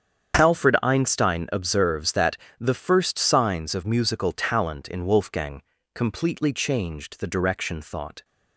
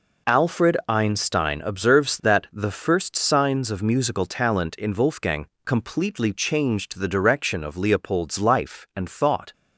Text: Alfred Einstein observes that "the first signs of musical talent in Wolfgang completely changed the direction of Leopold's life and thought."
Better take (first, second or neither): second